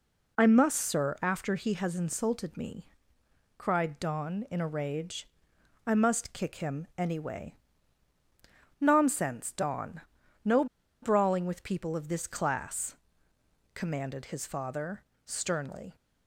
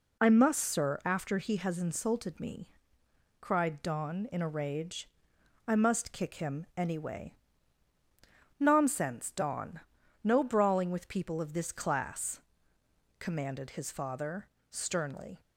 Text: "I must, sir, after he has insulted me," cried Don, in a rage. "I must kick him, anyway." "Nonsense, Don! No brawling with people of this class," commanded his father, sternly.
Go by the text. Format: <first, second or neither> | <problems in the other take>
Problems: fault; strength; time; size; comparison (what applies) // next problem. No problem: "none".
second | pauses between "No" and "brawling"; at 10.6 s; 0.37 s long